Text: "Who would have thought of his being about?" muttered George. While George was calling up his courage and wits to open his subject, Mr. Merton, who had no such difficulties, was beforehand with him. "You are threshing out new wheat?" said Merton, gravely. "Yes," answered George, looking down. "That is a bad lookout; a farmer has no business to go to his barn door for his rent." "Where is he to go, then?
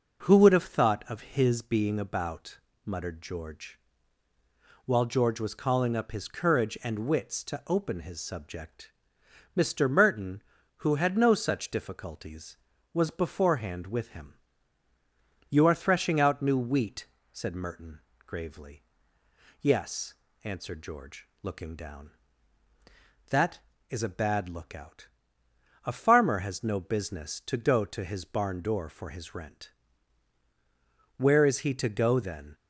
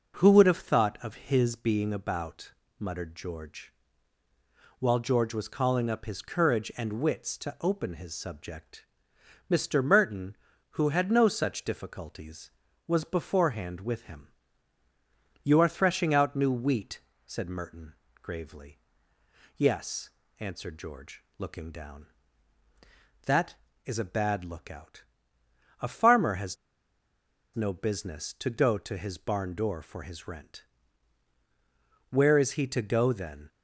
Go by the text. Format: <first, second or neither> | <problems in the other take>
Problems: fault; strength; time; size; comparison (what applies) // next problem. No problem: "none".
first | pauses between "has" and "no"; at 26.5 s; 0.98 s long